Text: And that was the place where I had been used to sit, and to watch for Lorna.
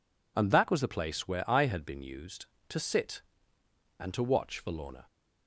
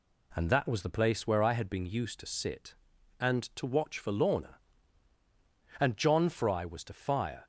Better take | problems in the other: first | goes on to say "And John Fry was to fire"; from 5.7 s on; 1.6 s long

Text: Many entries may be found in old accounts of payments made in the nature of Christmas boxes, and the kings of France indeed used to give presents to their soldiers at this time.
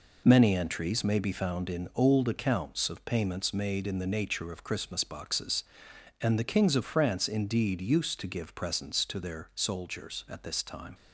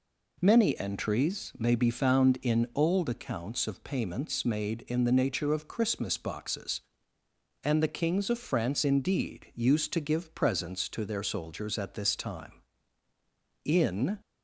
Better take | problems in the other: first | goes on to say "In"; from 13.6 s on; 0.56 s long

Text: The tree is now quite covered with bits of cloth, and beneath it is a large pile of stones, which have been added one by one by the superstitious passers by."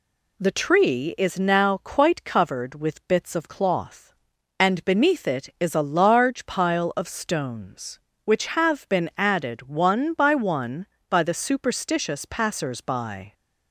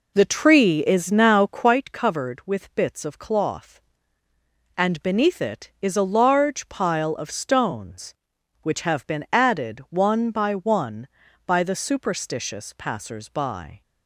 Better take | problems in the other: first | starts louder than the rest; until 1.8 s; 4 dB

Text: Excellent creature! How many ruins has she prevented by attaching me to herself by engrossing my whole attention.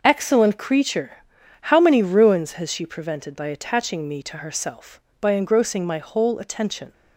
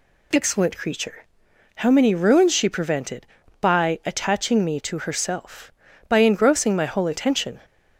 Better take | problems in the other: first | skips "has"; at 2.5 s

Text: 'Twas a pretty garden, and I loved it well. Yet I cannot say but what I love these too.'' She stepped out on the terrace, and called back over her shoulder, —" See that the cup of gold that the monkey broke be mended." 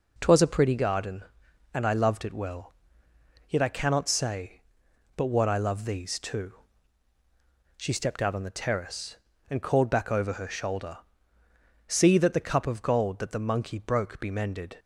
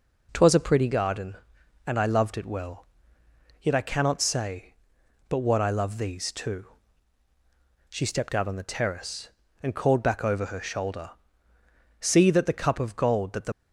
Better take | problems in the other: first | stops before "monkey broke be mended"; at 13.5 s

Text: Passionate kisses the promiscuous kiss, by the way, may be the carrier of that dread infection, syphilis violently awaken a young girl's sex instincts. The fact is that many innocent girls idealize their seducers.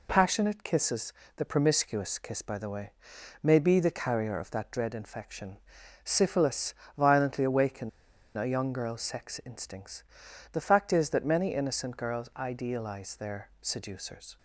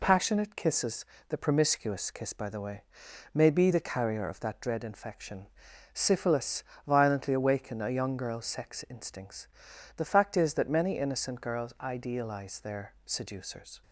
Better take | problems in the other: second | pauses between "kisses" and "the"; slight; at 1.1 s; 0.24 s long; slight in the second // pauses between "syphilis" and "violently"; slight; at 6.7 s; 0.24 s long; slight in the second // pauses between "awaken" and "a"; noticeable; at 7.8 s; 0.48 s long

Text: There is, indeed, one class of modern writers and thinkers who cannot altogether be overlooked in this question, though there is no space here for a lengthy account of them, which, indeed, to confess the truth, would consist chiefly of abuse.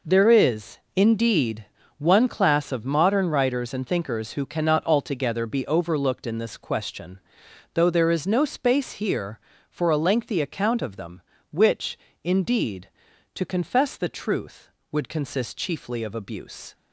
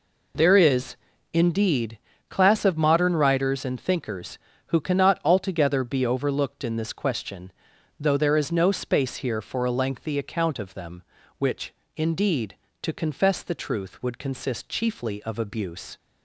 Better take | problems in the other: first | skips "one"; at 2.1 s

